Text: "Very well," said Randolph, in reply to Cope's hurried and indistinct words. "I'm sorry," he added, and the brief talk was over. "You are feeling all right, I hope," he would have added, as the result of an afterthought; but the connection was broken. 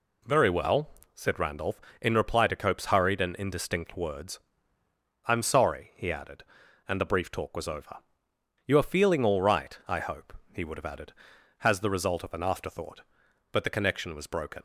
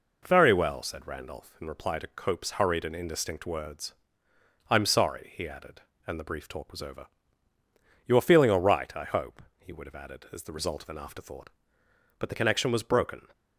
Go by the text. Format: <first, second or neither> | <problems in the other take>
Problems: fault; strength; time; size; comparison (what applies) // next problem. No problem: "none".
second | says "has" for "as"; at 11.5 s